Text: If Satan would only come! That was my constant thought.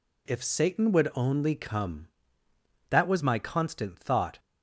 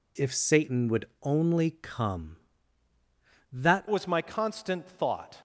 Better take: first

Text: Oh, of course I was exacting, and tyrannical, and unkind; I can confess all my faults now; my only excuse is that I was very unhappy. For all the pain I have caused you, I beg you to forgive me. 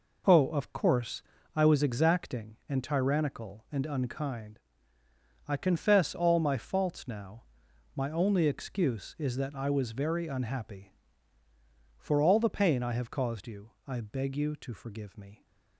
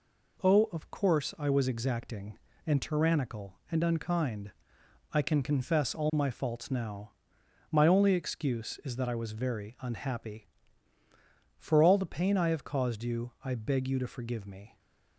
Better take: second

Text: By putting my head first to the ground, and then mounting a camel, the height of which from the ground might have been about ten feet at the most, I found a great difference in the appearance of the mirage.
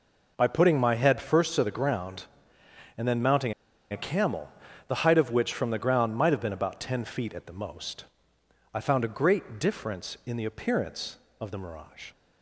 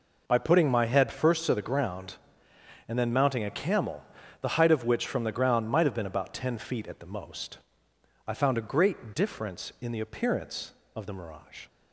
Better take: second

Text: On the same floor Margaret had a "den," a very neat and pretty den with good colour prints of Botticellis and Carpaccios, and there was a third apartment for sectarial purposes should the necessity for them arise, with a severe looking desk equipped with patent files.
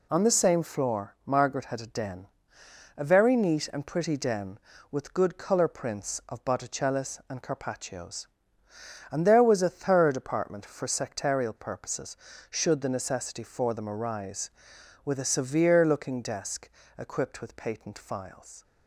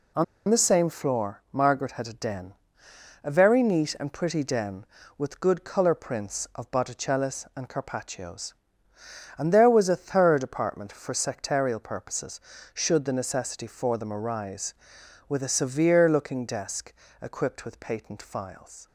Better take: first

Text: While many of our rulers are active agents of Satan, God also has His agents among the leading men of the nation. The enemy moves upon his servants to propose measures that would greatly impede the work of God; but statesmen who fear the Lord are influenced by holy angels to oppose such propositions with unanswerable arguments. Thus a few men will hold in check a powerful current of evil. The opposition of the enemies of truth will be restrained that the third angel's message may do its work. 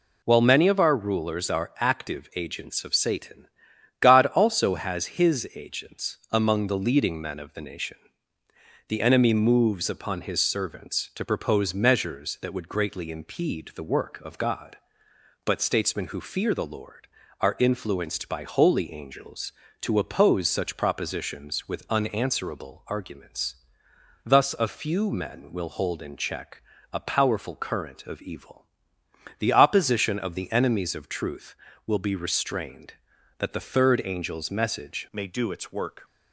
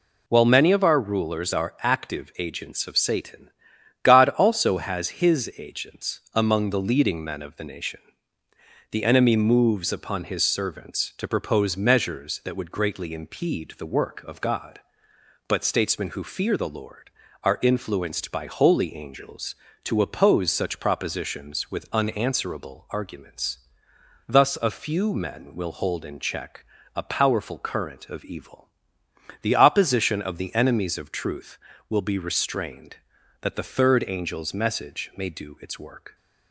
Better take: second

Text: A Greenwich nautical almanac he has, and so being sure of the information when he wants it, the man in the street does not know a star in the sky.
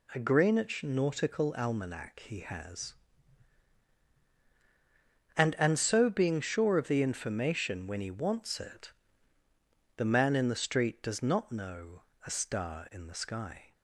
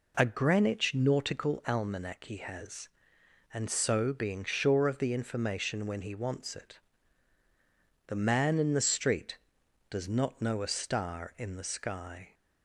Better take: second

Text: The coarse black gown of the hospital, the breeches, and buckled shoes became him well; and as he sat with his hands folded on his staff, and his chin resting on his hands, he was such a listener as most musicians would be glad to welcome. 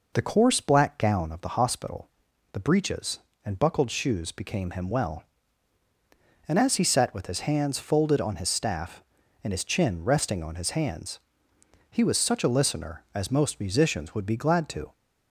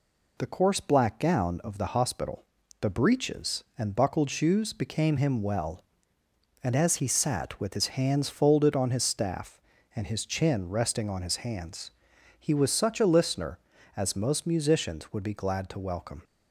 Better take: second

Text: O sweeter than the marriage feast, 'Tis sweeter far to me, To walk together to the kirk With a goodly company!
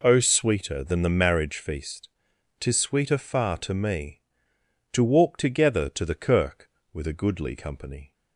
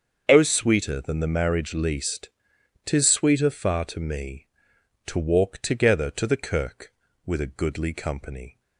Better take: first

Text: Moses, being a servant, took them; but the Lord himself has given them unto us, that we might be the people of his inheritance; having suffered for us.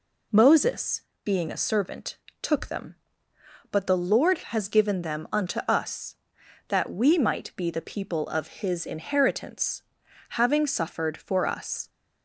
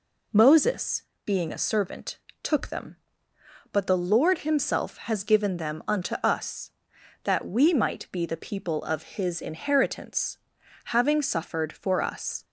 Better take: second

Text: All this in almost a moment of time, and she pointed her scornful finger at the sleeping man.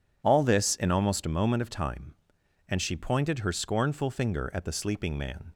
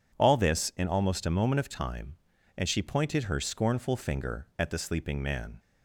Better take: neither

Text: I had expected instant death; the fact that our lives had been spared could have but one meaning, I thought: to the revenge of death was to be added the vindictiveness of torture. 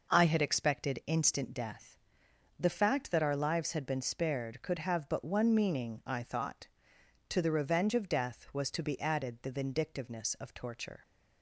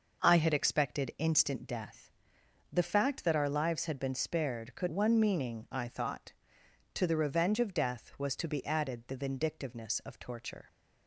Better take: first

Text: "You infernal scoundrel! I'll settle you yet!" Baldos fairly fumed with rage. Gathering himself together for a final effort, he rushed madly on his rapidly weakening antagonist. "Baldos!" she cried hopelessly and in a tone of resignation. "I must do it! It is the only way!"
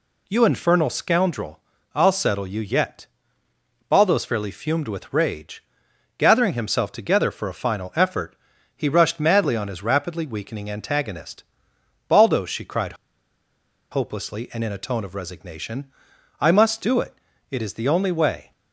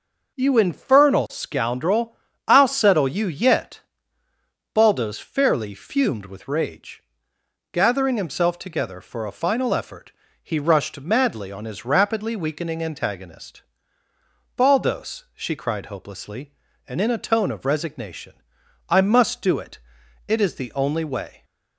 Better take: second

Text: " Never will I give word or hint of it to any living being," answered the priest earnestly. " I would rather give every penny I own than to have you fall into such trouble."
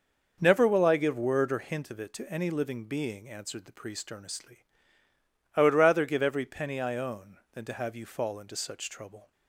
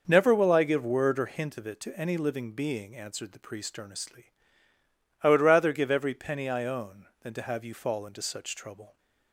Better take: neither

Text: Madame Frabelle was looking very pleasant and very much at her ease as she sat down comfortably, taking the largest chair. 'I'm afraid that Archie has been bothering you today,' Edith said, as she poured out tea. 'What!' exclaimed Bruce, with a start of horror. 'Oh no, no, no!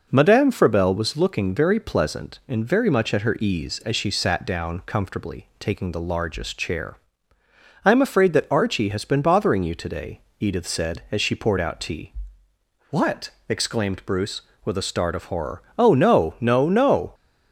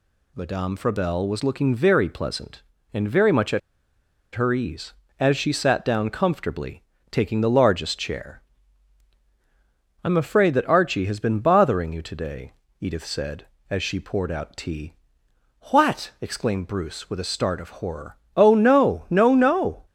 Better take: first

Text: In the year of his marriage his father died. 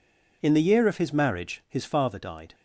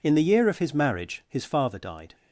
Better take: neither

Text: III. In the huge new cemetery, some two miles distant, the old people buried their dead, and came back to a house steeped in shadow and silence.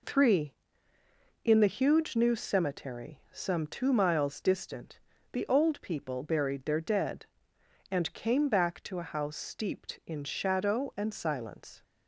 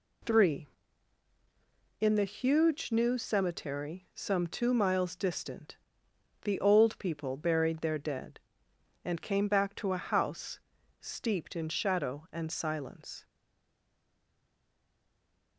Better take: first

